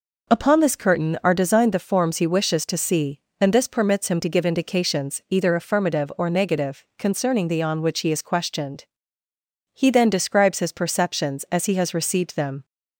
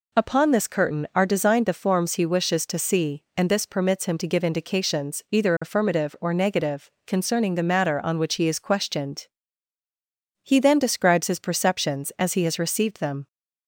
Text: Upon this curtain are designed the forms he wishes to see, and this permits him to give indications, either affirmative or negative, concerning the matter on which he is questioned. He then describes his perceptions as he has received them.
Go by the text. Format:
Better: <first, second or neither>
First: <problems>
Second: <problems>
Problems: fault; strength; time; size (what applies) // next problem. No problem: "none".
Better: second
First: skips "matter"; at 7.6 s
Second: none